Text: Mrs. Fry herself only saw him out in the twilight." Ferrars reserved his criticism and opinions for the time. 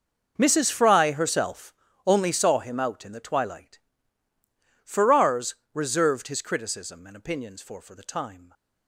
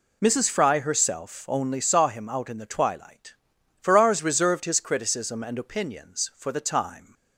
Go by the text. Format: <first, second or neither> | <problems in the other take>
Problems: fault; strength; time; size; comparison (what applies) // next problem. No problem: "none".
second | pauses between "herself" and "only"; slight; at 1.7 s; 0.32 s long // pauses between "Ferrars" and "reserved"; slight; at 5.5 s; 0.18 s long // says "for" twice; at 7.7 s